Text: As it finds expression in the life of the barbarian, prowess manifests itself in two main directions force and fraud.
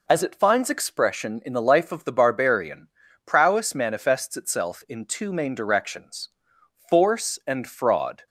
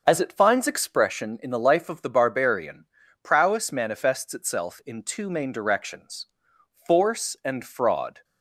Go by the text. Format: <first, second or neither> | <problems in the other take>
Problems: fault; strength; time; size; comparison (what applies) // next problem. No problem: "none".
first | starts louder than the rest; until 1.3 s; 6.5 dB // pauses between "directions" and "force"; noticeable; at 6.2 s; 0.60 s long; noticeable in the first